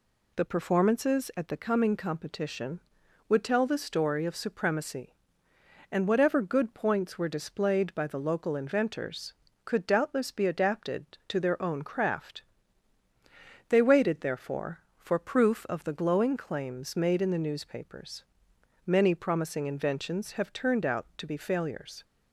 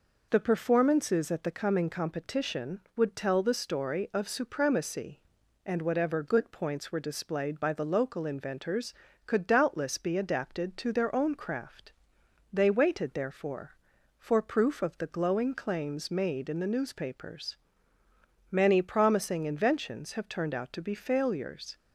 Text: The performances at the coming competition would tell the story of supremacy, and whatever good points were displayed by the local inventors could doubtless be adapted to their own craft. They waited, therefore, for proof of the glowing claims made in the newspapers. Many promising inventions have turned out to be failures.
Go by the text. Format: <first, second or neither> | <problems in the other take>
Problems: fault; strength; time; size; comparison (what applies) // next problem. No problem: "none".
neither | none